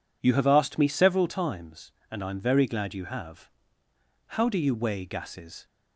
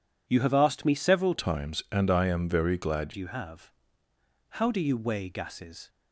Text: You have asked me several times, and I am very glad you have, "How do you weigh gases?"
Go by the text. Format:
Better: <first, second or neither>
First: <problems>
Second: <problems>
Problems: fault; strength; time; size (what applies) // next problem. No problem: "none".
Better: first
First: none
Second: changes voice from "times" to "glad"; from 1.3 to 3.1 s; 1.8 s long